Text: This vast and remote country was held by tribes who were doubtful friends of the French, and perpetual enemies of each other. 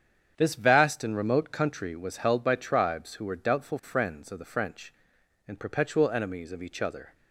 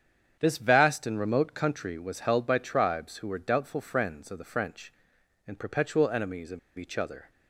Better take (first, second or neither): first